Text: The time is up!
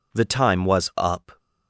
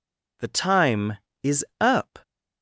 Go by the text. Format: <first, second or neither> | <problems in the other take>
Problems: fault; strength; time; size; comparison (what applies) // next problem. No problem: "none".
second | says "was" for "is"; at 0.6 s